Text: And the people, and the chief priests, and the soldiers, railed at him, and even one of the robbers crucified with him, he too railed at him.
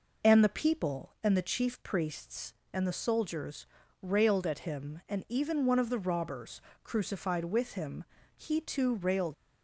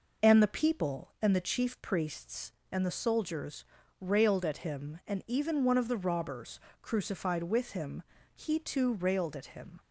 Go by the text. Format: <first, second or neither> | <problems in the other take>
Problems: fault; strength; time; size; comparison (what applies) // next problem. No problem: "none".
second | pauses between "robbers" and "crucified"; slight; at 6.6 s; 0.22 s long; slight in the second // stops before "at him"; at 9.3 s